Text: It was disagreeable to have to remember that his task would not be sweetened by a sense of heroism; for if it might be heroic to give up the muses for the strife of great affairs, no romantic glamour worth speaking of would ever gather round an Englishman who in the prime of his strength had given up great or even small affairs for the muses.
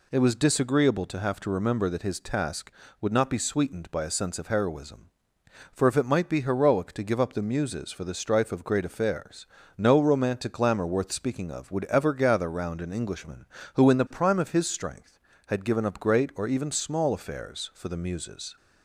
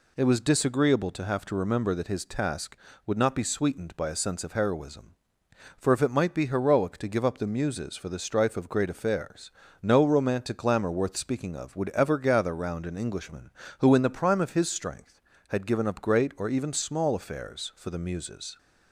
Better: neither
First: none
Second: none

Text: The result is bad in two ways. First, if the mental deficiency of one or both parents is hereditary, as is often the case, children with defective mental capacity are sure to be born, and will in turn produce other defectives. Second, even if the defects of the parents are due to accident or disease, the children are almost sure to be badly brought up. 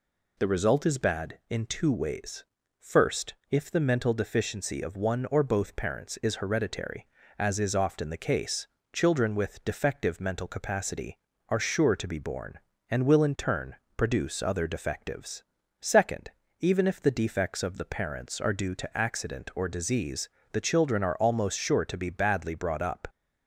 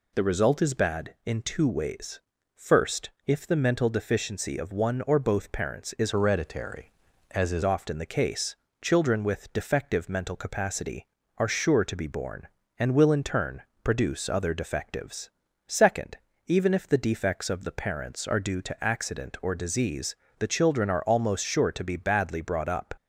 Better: first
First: pauses between "turn" and "produce"; slight; at 13.7 s; 0.22 s long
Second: changes voice from "hereditary" to "is"; from 6.1 to 7.6 s; 1.5 s long // pauses between "turn" and "produce"; slight; at 13.6 s; 0.22 s long

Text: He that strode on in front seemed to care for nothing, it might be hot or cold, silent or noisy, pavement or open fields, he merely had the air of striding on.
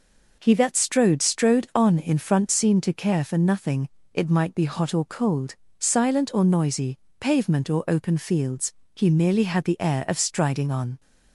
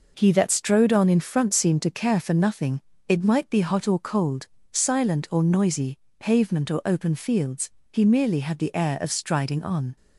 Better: second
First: says "strode" twice; at 1.2 s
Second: none

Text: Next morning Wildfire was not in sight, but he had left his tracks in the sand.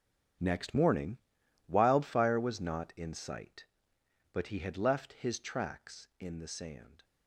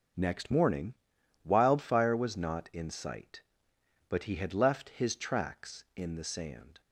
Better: second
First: gets quieter; strong; throughout; 15.5 dB // pauses between "morning" and "Wildfire"; noticeable; at 1.1 s; 0.50 s long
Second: pauses between "morning" and "Wildfire"; noticeable; at 0.9 s; 0.50 s long

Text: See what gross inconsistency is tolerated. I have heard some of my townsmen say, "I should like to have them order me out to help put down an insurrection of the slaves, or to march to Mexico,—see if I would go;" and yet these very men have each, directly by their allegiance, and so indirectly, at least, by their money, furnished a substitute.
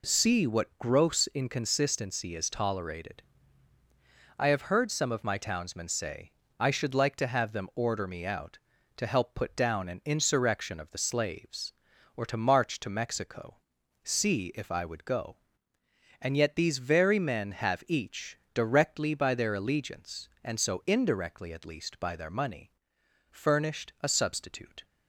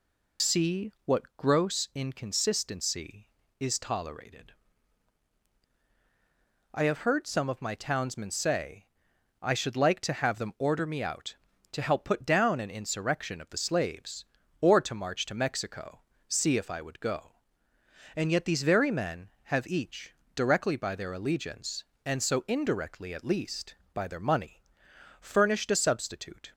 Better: first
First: none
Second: loses the start of "See"; at 0.3 s; 90 ms

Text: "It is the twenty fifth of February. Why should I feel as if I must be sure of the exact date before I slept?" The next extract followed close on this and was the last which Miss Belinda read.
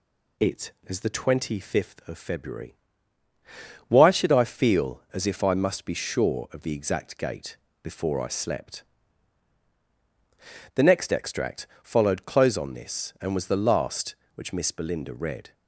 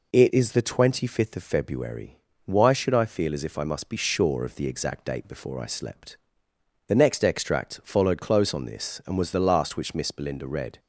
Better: second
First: says "gate" for "date"; at 7.1 s // pauses between "extract" and "followed"; slight; at 11.6 s; 0.18 s long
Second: none

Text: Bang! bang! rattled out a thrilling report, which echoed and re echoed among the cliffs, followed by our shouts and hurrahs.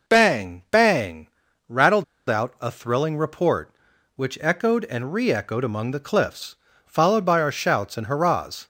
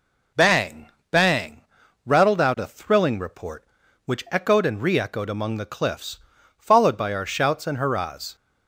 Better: second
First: pauses between "rattled" and "out"; slight; at 2.0 s; 0.24 s long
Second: none

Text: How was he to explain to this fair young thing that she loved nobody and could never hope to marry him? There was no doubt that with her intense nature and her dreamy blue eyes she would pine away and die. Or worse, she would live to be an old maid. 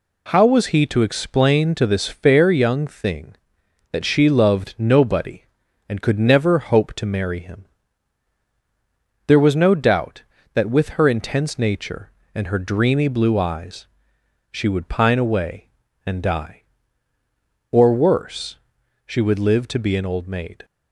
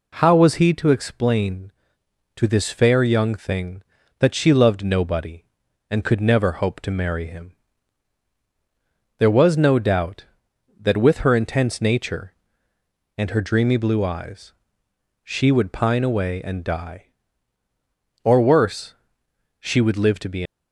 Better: first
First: pauses between "eyes" and "she"; noticeable; at 13.8 s; 0.64 s long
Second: pauses between "eyes" and "she"; noticeable; at 14.5 s; 0.70 s long // stops before "an old maid"; at 20.4 s

